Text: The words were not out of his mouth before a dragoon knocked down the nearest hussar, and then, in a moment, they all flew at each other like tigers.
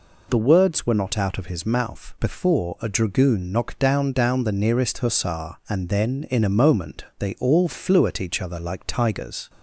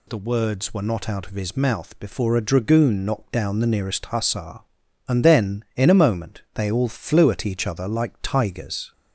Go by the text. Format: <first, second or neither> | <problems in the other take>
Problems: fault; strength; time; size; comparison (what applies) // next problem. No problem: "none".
second | says "down" twice; at 4.1 s